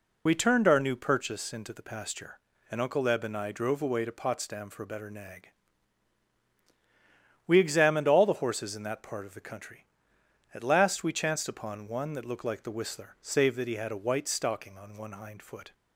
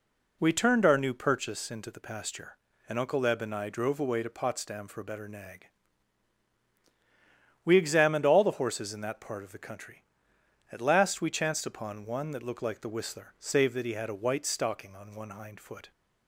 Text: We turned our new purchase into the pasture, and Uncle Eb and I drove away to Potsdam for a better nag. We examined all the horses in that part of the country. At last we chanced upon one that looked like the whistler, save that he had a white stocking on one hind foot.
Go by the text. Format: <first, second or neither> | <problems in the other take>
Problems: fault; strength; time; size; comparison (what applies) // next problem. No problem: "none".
second | loses the start of "We"; at 0.2 s; 30 ms